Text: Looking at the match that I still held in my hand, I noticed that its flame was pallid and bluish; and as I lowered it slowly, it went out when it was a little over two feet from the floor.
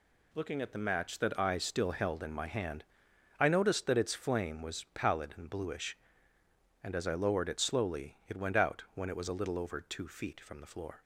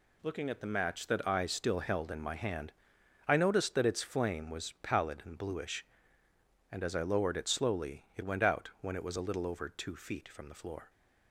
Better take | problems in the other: neither | none

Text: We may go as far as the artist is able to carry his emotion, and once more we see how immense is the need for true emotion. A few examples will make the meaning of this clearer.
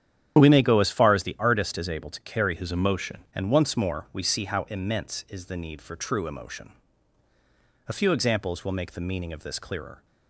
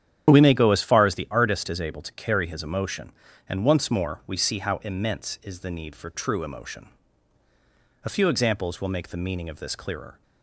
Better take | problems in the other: second | starts louder than the rest; strong; until 1.4 s; 9.5 dB; strong in the second // changes voice from "his" to "emotion"; from 2.5 to 3.2 s; 0.7 s long

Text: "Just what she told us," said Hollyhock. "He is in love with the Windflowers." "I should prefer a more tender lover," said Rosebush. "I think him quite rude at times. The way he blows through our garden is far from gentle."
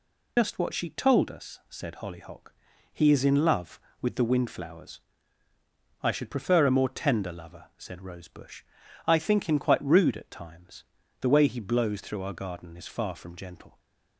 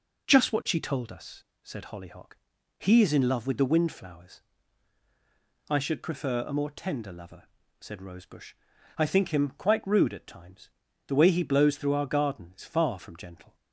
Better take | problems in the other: second | loses the start of "Just"; at 0.3 s; 130 ms

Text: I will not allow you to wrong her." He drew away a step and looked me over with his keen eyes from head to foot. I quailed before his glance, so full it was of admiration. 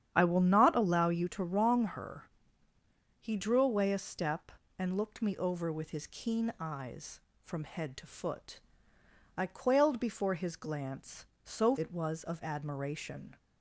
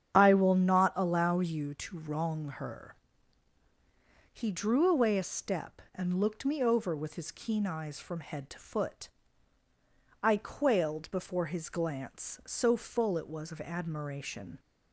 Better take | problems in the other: second | starts louder than the rest; strong; until 1.1 s; 9 dB; strong in the second // skips "full"; at 11.7 s

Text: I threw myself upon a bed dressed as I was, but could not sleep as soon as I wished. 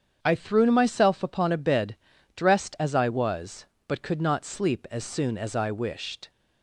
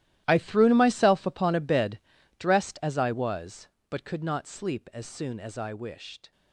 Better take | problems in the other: first | gets quieter; strong; throughout; 16 dB // starts louder than the rest; strong; until 1.2 s; 14 dB; strong in the first // pauses between "bed" and "dressed"; at 1.9 s; 0.38 s long; also in the first

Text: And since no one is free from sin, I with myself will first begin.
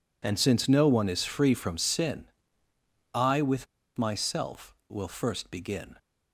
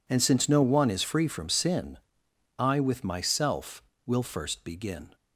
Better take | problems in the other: second | pauses between "with" and "myself"; slight; at 3.6 s; 0.30 s long

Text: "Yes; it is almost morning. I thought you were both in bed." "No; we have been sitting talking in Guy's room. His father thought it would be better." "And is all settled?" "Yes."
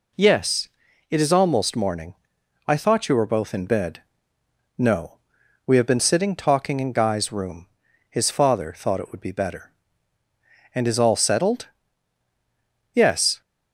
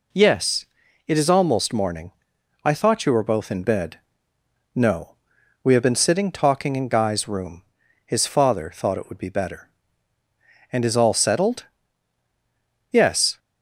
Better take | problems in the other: neither | none

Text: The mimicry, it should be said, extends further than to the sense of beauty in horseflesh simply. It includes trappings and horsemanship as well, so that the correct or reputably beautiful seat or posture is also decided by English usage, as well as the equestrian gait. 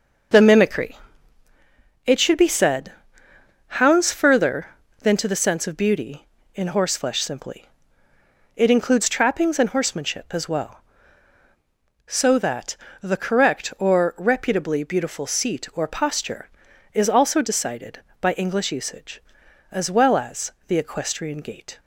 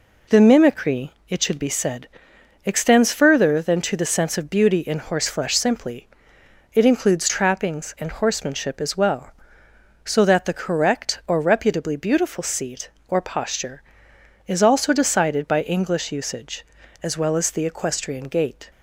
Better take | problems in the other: second | starts louder than the rest; until 2.4 s; 6.5 dB // says "hounds" for "extends"; at 3.6 s // pauses between "that" and "the"; slight; at 12.7 s; 0.24 s long // pauses between "as" and "the"; slight; at 20.5 s; 0.16 s long

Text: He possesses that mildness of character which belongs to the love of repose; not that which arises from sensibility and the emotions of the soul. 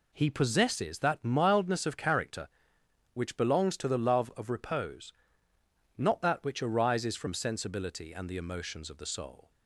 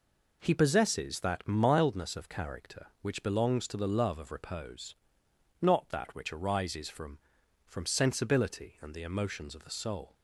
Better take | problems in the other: first | says "from" twice; at 7.6 s

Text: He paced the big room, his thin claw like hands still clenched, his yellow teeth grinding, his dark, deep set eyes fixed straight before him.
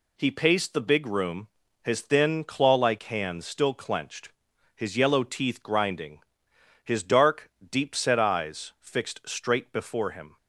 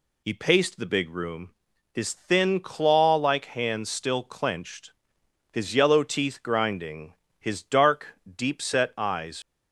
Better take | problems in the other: first | stops before "fixed straight before him"; at 9.4 s

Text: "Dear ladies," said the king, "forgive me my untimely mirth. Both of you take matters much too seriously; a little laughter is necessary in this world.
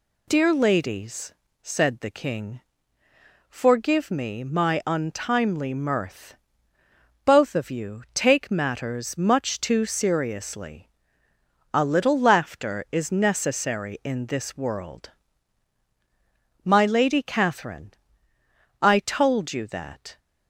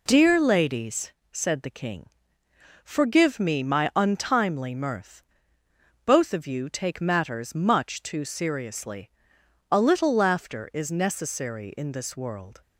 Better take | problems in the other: second | goes on to say "My Lady Catherine I told you that"; strong; from 16.6 s on; 3.5 s long

